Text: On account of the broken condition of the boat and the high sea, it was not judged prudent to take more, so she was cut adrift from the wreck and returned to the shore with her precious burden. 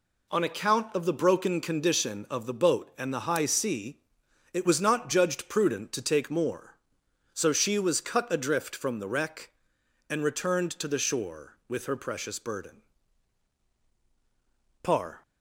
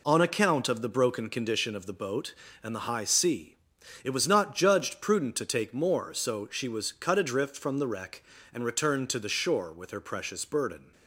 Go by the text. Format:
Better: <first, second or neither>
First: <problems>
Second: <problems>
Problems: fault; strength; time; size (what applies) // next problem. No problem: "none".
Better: second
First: goes on to say "par"; slight; from 14.8 s on; 0.40 s long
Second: none